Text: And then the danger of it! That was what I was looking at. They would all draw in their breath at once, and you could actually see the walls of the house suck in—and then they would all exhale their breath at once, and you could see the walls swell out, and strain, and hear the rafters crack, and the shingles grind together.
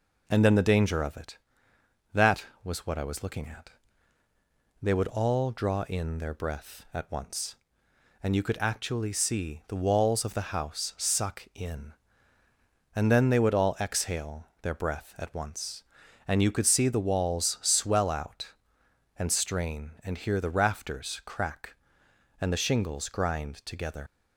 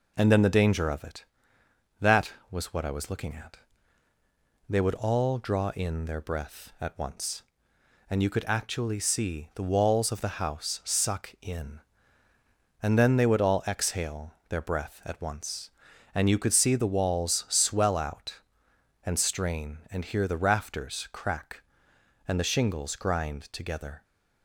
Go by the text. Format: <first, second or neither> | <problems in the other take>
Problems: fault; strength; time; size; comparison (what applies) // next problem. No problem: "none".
second | pauses between "exhale" and "their"; slight; at 14.4 s; 0.18 s long; slight in the second // leaves "together" unfinished; at 24.0 s; 100 ms